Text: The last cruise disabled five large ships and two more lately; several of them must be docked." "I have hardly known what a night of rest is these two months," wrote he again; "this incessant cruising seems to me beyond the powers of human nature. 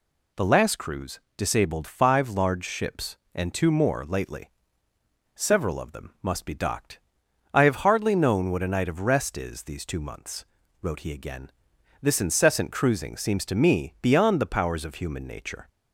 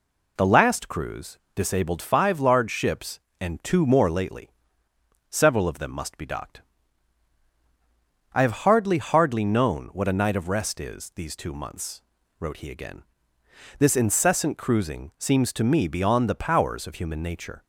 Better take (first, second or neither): first